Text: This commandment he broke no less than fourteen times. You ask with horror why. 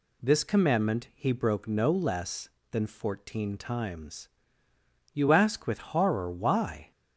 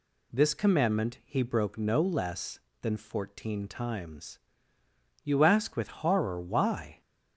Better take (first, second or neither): neither